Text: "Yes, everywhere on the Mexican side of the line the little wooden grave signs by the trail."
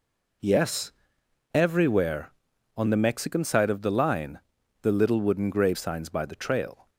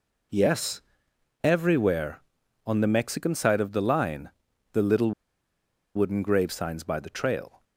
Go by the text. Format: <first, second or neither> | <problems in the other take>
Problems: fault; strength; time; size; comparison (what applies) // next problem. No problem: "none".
first | pauses between "line" and "the"; at 4.3 s; 0.40 s long; also in the first // pauses between "little" and "wooden"; noticeable; at 5.1 s; 0.83 s long